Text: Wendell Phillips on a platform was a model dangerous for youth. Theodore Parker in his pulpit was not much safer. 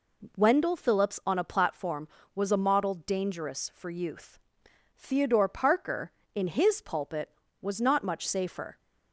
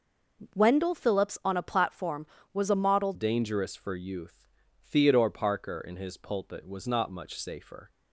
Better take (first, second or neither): first